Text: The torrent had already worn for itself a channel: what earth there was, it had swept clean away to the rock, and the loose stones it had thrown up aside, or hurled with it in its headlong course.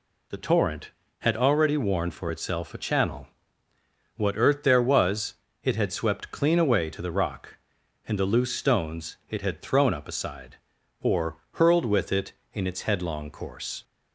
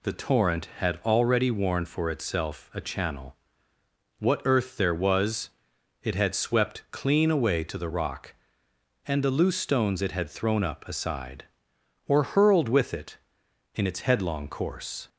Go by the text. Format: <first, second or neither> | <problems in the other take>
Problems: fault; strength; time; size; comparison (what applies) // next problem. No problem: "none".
neither | none